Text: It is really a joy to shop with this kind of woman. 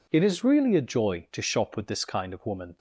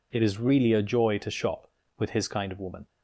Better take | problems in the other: first | says "his" for "this"; at 2.1 s

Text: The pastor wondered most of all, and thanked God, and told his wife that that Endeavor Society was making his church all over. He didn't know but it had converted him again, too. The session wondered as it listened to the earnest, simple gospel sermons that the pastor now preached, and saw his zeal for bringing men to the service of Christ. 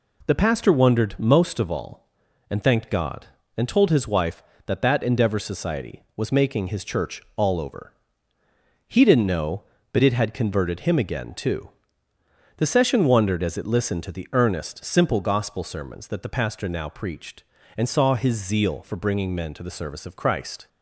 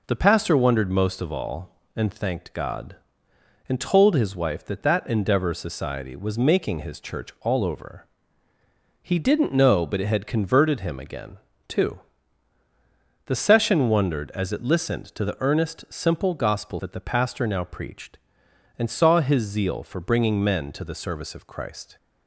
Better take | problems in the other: first | skips "sermons"; at 16.7 s

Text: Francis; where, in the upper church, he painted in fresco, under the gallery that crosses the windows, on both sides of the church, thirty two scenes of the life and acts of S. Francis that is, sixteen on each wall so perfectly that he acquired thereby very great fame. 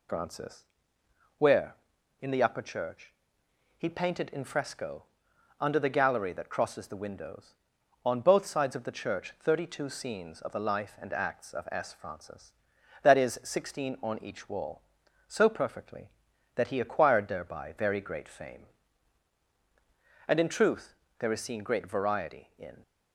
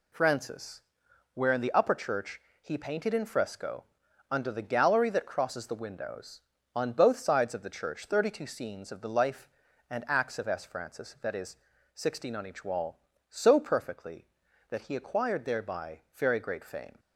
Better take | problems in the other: second | goes on to say "And in truth there is seen great variety in"; strong; from 20.2 s on; 2.5 s long

